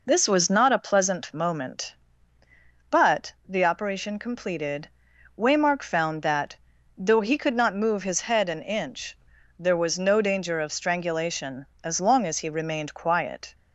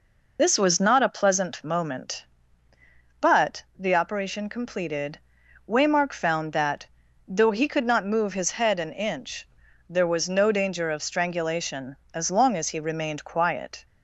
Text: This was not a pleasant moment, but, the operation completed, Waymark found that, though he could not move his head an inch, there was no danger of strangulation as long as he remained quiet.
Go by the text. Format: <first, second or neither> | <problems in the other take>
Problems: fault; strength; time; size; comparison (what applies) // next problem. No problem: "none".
first | loses the start of "This"; at 0.3 s; 25 ms